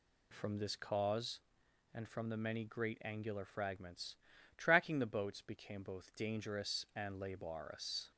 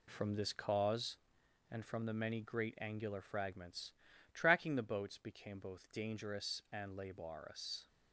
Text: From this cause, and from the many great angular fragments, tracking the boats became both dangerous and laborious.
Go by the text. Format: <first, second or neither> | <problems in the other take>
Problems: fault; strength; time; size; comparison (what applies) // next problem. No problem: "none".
first | gets quieter; throughout; 6.5 dB